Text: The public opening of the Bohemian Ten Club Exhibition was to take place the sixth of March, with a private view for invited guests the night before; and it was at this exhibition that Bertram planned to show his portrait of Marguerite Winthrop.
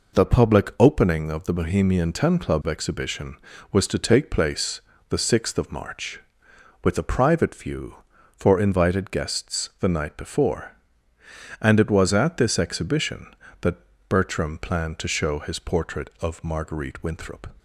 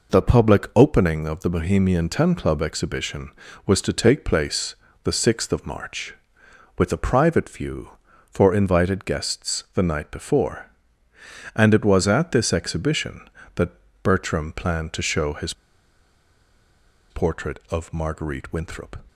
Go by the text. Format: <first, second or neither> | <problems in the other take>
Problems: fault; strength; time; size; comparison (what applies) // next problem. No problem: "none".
first | pauses between "place" and "the"; slight; at 4.7 s; 0.30 s long; slight in the first // pauses between "that" and "Bertram"; slight; at 13.7 s; 0.32 s long; slight in the first // pauses between "his" and "portrait"; strong; at 15.5 s; 1.5 s long